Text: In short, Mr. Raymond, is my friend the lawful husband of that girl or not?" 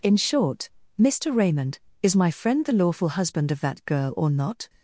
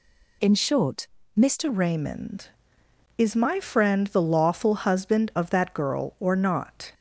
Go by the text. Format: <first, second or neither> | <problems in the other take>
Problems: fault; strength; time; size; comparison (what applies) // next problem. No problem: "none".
first | changes voice at "Raymond"; from 1.6 s on; 5.3 s long